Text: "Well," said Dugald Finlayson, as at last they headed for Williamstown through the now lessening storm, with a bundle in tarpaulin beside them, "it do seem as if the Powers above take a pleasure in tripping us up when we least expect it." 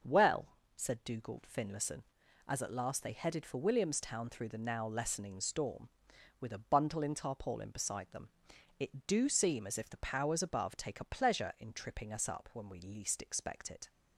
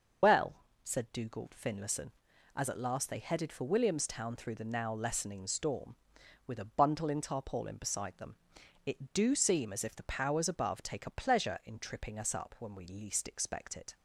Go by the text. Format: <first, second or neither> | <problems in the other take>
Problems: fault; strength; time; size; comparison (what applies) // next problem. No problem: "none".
first | loses the start of "Well"; at 0.2 s; 115 ms // starts louder than the rest; until 1.5 s; 6 dB; also in the first